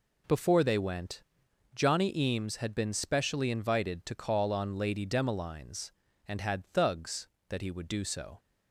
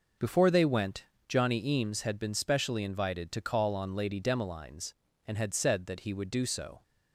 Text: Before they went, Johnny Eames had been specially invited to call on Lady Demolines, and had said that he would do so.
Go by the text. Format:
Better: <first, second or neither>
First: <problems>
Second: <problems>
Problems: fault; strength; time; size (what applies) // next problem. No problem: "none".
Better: second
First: says "thugs" for "said"; at 6.6 s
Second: none